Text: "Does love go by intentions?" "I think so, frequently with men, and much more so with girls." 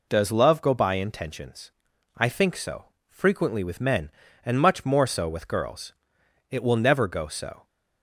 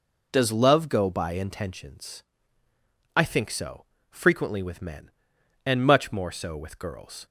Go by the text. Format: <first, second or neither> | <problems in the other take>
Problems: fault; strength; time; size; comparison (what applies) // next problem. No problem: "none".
second | goes on to say "It will never go so"; noticeable; from 6.4 s on; 1.1 s long